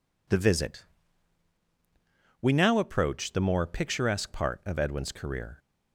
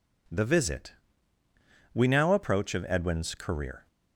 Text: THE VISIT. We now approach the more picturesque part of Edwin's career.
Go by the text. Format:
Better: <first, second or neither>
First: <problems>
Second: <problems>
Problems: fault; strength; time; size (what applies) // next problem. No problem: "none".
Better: first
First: none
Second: skips "the more picturesque part"; at 2.7 s